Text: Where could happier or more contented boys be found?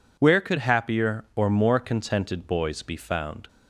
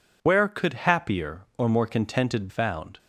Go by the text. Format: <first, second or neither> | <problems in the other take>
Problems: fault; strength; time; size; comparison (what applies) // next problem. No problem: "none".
first | skips "boys be"; at 2.4 s